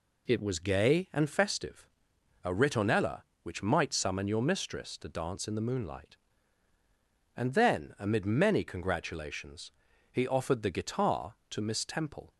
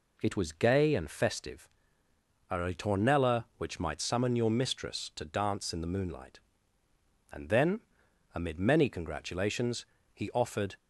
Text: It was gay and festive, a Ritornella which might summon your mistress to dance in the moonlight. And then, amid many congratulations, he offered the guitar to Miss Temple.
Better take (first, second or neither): first